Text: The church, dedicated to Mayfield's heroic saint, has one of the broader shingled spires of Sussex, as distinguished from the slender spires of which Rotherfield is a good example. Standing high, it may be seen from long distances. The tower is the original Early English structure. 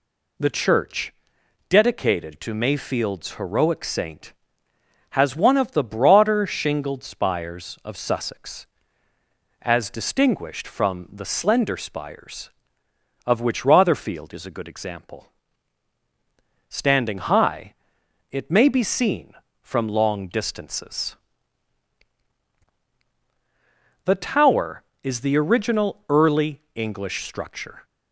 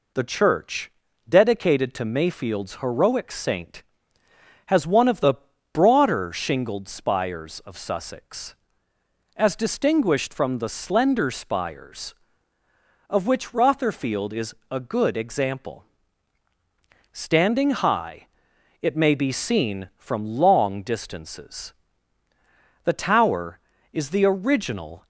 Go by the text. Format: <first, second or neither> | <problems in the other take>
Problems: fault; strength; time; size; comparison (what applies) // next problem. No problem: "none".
first | pauses between "the" and "broader"; at 5.3 s; 0.38 s long // pauses between "is" and "a"; slight; at 14.5 s; 0.16 s long // stops before "Early English structure"; at 25.0 s